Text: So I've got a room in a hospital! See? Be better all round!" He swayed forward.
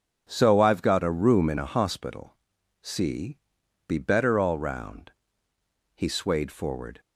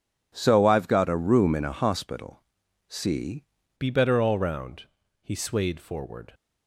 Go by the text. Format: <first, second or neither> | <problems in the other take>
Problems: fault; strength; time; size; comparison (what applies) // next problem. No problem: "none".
first | changes voice at "Be"; from 3.7 s on; 2.6 s long